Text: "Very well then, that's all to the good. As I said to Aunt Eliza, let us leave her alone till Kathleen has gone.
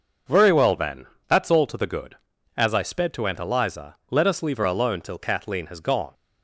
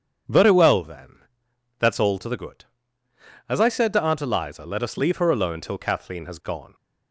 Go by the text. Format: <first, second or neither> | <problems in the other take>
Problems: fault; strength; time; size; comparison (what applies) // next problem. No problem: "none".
second | says "sped" for "said"; at 2.8 s